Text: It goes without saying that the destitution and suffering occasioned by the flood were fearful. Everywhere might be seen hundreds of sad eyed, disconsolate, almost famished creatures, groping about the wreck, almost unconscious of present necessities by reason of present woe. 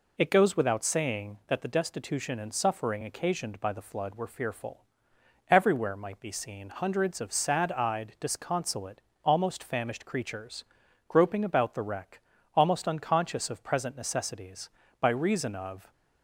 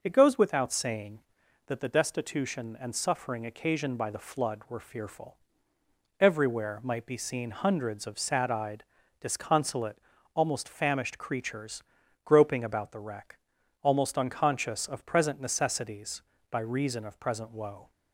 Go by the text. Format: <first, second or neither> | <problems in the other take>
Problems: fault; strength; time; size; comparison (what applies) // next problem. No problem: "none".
second | stops before "present woe"; at 15.9 s